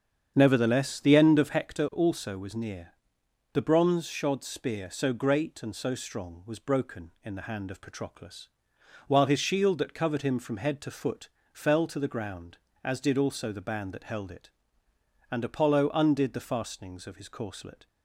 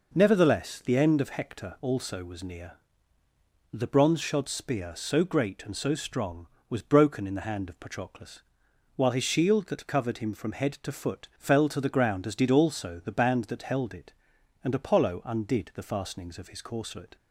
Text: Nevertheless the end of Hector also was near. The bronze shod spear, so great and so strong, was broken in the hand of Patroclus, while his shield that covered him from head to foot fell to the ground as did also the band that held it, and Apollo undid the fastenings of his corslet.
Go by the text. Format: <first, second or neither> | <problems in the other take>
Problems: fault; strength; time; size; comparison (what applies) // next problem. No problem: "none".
second | starts louder than the rest; strong; until 1.8 s; 7.5 dB // pauses between "foot" and "fell"; slight; at 11.2 s; 0.24 s long